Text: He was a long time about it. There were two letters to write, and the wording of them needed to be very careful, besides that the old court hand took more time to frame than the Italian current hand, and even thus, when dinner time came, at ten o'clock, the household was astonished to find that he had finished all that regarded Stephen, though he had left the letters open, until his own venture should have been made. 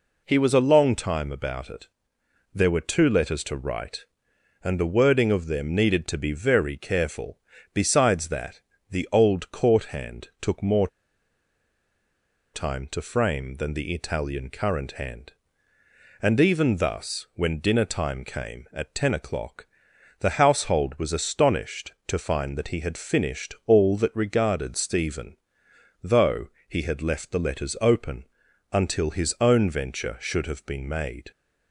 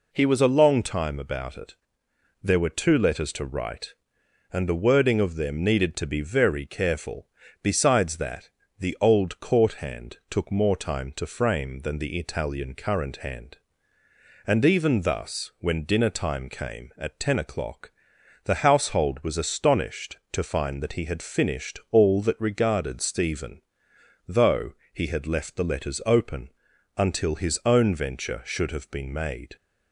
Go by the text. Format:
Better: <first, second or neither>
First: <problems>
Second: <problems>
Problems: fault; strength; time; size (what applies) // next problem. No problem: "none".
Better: second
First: pauses between "that" and "the"; slight; at 8.6 s; 0.28 s long // pauses between "more" and "time"; strong; at 10.8 s; 1.6 s long // pauses between "though" and "he"; slight; at 26.4 s; 0.18 s long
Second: pauses between "that" and "the"; slight; at 8.4 s; 0.28 s long // pauses between "though" and "he"; slight; at 24.7 s; 0.18 s long